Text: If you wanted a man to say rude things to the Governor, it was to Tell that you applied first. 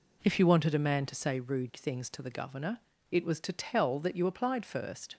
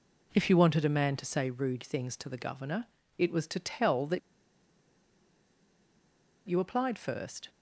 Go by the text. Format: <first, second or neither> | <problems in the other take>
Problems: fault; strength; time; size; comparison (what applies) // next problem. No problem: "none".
first | pauses between "that" and "you"; strong; at 4.1 s; 2.2 s long